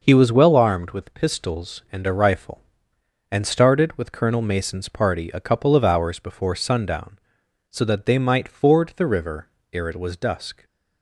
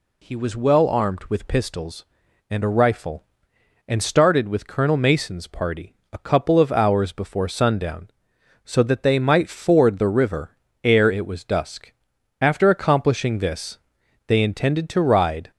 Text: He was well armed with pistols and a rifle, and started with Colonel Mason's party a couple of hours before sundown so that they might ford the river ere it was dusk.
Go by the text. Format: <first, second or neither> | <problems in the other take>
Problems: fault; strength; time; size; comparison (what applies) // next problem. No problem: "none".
first | pauses between "party" and "a"; slight; at 5.9 s; 0.18 s long // pauses between "river" and "ere"; slight; at 10.5 s; 0.28 s long; slight in the first // goes on to say "After accomplishing this they intended to ride"; strong; from 12.4 s on; 3.1 s long